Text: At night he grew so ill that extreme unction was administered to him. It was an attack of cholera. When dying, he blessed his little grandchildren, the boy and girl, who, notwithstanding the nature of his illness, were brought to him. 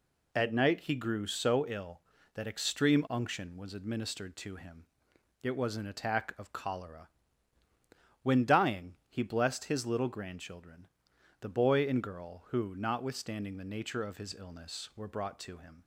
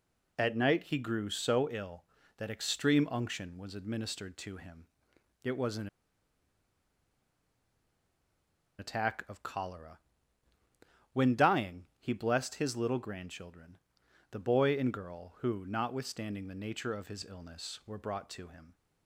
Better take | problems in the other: first | pauses between "an" and "attack"; strong; at 5.8 s; 2.9 s long

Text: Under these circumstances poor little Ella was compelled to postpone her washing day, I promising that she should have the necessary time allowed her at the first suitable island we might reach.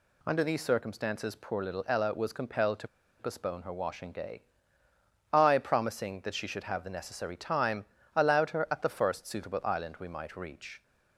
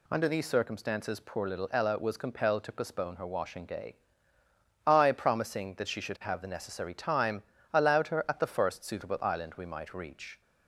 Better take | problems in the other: second | pauses between "to" and "postpone"; slight; at 2.8 s; 0.31 s long // pauses between "time" and "allowed"; slight; at 7.8 s; 0.28 s long; slight in the second

